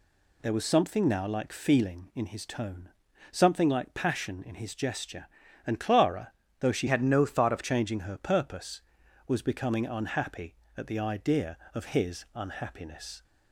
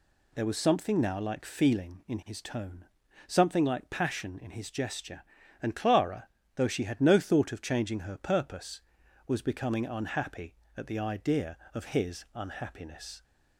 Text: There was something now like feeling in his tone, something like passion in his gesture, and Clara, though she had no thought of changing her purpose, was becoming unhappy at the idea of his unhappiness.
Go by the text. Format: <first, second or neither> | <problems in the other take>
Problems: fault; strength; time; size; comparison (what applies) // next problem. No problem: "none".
second | changes voice from "had" to "of"; from 6.8 to 7.6 s; 0.8 s long